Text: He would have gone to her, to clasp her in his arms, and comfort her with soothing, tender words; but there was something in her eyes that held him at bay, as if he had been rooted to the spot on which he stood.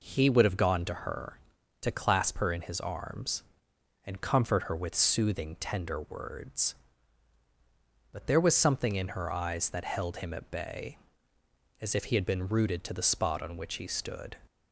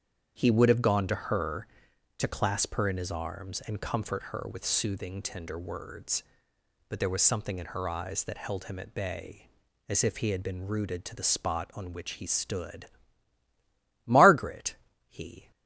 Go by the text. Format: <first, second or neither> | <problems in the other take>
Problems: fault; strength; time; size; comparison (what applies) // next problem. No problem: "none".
first | starts louder than the rest; strong; until 1.3 s; 7.5 dB // goes on to say "Margaret he"; from 14.0 s on; 1.4 s long